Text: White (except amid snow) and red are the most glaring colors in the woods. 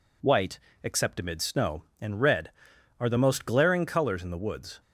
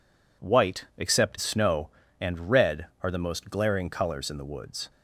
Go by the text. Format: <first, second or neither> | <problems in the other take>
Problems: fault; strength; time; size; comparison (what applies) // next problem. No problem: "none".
first | skips "amid"; at 1.3 s